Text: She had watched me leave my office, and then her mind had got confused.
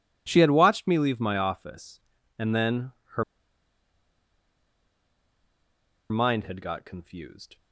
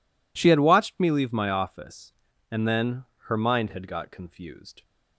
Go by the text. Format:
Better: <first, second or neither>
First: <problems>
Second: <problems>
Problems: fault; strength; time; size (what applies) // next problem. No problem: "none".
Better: second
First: pauses between "then" and "her"; slight; at 2.9 s; 0.24 s long // pauses between "her" and "mind"; strong; at 3.2 s; 2.8 s long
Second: pauses between "then" and "her"; slight; at 3.0 s; 0.24 s long